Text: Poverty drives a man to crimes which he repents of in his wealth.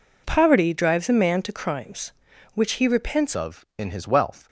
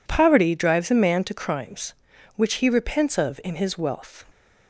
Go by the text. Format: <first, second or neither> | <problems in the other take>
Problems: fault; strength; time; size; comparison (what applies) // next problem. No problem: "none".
second | changes voice at "of"; from 3.3 s on; 1.1 s long